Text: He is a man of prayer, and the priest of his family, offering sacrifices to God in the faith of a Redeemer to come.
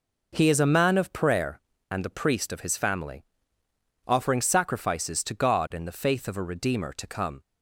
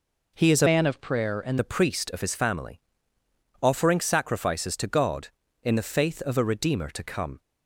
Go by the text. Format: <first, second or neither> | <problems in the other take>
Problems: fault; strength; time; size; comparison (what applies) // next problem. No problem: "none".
first | changes voice from "man" to "and"; from 0.6 to 1.5 s; 0.9 s long